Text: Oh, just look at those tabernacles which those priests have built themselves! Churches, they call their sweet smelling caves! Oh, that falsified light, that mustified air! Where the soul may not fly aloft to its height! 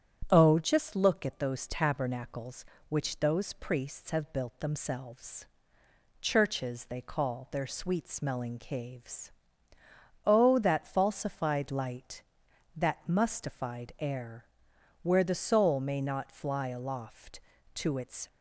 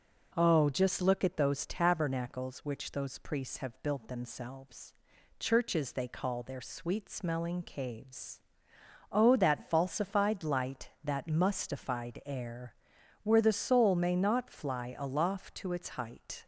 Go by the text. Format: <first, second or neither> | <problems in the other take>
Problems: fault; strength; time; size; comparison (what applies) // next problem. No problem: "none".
second | starts louder than the rest; strong; until 1.3 s; 9 dB // stops before "height"; at 18.2 s